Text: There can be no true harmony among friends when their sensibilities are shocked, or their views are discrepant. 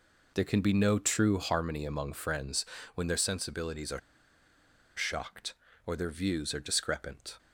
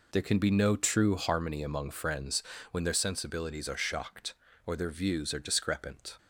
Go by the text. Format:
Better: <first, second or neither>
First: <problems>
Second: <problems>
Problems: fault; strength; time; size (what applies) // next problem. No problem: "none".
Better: second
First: pauses between "friends" and "when"; slight; at 2.6 s; 0.30 s long // pauses between "are" and "shocked"; noticeable; at 3.9 s; 0.97 s long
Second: pauses between "friends" and "when"; slight; at 2.4 s; 0.29 s long